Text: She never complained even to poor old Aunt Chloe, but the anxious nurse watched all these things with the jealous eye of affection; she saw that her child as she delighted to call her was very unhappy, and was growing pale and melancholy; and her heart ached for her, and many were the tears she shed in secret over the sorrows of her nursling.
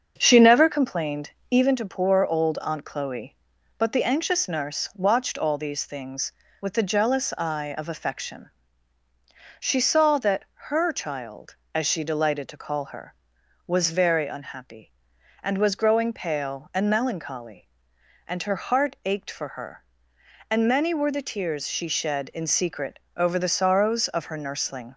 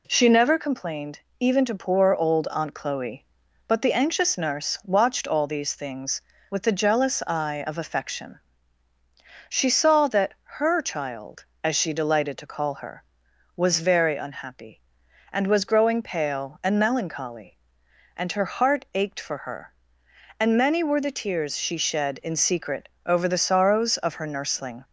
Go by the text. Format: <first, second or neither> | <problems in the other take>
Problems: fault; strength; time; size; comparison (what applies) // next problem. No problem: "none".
second | starts louder than the rest; until 1.7 s; 7 dB // pauses between "complained" and "even"; slight; at 1.2 s; 0.22 s long; slight in the second // pauses between "secret" and "over"; slight; at 22.9 s; 0.18 s long; slight in the second